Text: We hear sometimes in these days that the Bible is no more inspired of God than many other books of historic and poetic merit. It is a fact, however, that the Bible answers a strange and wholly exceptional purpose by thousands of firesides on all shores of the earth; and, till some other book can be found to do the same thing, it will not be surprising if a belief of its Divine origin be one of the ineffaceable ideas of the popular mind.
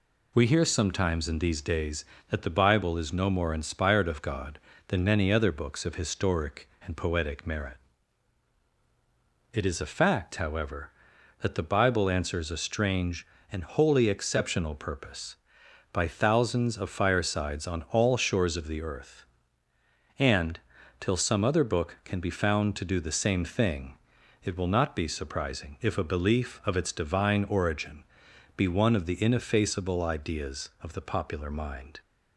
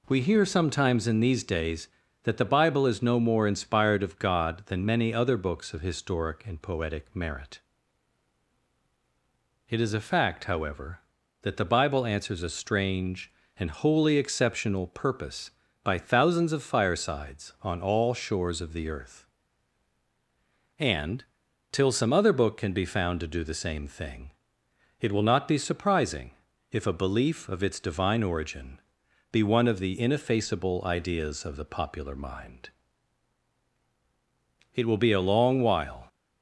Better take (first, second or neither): first